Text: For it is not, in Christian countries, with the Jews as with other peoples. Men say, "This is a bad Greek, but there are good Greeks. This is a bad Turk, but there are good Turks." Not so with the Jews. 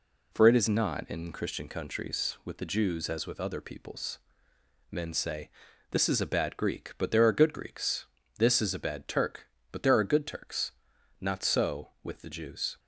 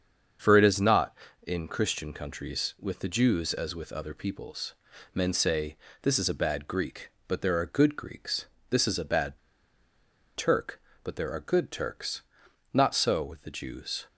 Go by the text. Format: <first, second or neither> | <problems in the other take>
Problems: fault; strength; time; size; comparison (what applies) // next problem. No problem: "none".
first | starts louder than the rest; strong; until 1.7 s; 7 dB // pauses between "bad" and "Turk"; noticeable; at 9.3 s; 0.96 s long